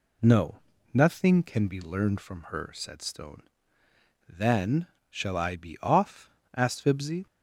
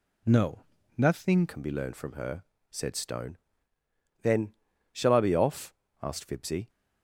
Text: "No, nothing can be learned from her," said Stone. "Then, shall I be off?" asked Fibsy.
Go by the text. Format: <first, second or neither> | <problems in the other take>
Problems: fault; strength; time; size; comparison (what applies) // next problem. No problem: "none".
first | changes voice at "can"; from 1.4 s on; 5.2 s long